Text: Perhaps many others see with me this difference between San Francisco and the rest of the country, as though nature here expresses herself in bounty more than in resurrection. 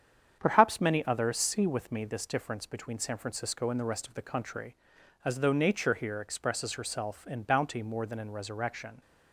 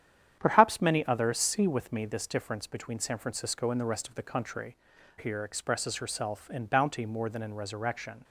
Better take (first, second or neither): first